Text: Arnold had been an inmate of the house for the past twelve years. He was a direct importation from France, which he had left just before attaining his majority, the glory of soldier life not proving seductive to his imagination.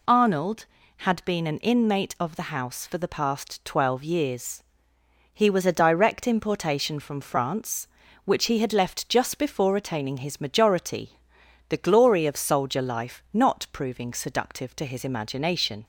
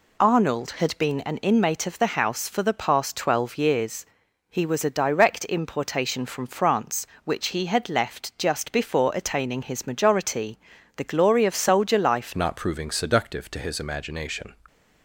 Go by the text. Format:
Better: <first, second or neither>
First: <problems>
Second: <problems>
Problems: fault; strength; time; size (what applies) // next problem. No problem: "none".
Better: first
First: none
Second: changes voice at "not"; from 12.3 s on; 2.2 s long